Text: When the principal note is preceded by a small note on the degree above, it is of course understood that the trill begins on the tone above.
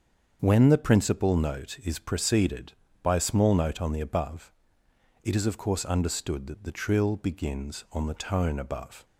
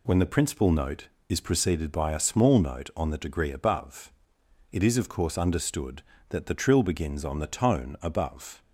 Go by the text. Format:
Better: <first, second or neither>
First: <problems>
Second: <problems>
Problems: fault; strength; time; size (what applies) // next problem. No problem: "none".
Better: second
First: starts louder than the rest; strong; until 1.4 s; 7 dB // skips "degree"; at 4.0 s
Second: none